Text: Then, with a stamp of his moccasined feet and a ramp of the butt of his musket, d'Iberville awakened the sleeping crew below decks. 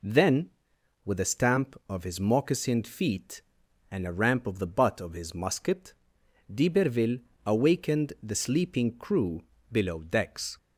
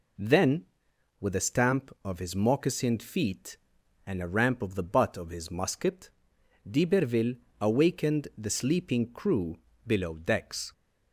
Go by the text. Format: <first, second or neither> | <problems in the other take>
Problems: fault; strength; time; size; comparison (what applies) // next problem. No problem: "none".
neither | pauses between "d'Iberville" and "awakened"; slight; the same in both // pauses between "crew" and "below"; slight; the same in both